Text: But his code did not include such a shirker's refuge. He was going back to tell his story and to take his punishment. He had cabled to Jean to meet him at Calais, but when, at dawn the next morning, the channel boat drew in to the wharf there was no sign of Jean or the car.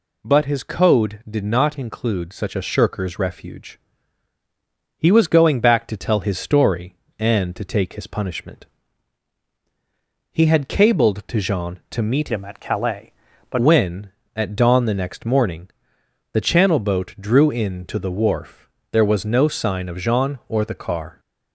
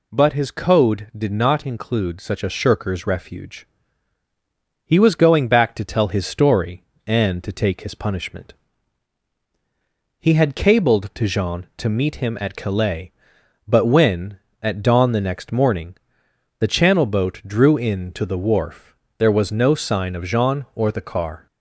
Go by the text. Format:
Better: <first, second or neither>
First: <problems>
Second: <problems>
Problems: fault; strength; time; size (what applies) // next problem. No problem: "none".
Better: second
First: changes voice from "him" to "but"; from 12.3 to 13.5 s; 1.2 s long // pauses between "wharf" and "there"; slight; at 18.6 s; 0.22 s long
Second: pauses between "wharf" and "there"; slight; at 18.9 s; 0.22 s long